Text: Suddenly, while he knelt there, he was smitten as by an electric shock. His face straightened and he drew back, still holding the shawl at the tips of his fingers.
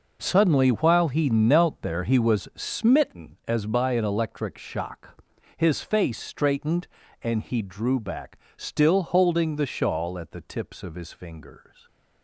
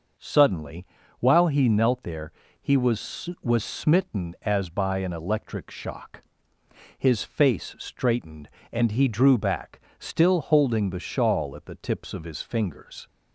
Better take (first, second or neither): first